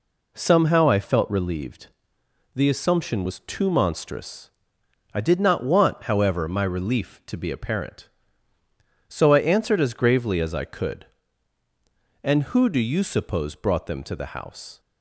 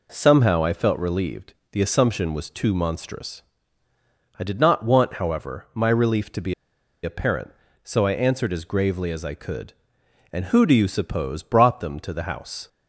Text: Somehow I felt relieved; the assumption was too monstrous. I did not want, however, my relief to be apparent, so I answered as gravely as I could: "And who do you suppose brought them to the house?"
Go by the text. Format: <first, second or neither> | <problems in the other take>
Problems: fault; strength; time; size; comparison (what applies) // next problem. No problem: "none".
first | pauses between "be" and "apparent"; noticeable; at 6.5 s; 0.50 s long